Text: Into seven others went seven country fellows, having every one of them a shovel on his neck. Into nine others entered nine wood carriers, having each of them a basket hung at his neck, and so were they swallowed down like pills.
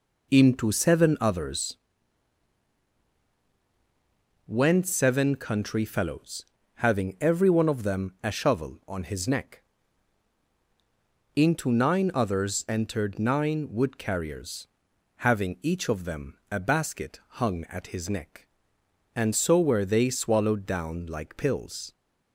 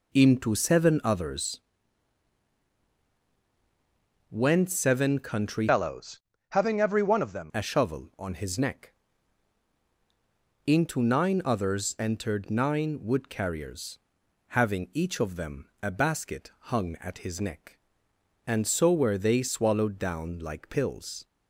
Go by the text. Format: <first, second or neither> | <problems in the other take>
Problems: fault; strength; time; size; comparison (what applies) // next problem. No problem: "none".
first | pauses between "others" and "went"; strong; at 1.6 s; 2.6 s long; strong in the first // changes voice from "fellows" to "them"; from 5.6 to 7.5 s; 1.9 s long // pauses between "them" and "a"; slight; at 15.6 s; 0.16 s long; slight in the first // pauses between "basket" and "hung"; slight; at 16.5 s; 0.22 s long; slight in the first